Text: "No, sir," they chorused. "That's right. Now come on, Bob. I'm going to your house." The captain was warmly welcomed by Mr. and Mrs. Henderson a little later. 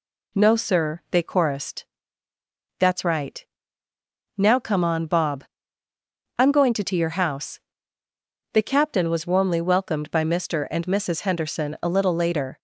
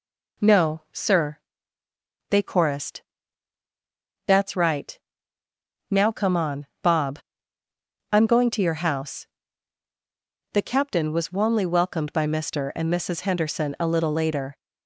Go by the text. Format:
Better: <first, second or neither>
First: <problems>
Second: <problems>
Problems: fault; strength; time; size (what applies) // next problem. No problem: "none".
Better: second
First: says "to" twice; at 6.8 s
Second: none